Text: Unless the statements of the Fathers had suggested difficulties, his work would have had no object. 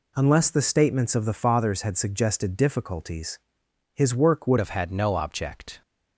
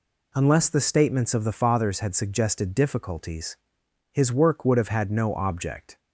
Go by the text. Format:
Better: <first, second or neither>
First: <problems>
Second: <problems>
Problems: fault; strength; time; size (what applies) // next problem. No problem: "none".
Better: second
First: changes voice at "have"; from 4.5 s on; 1.3 s long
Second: none